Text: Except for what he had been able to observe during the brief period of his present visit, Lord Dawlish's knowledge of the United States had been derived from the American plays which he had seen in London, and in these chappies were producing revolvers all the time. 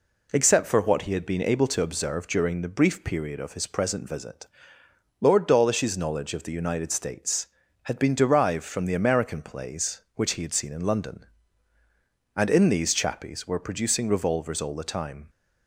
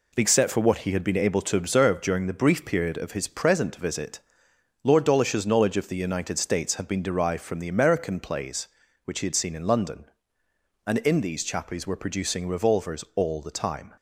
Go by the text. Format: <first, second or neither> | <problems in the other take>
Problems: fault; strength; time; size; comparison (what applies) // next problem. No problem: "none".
first | gets quieter; noticeable; throughout; 6 dB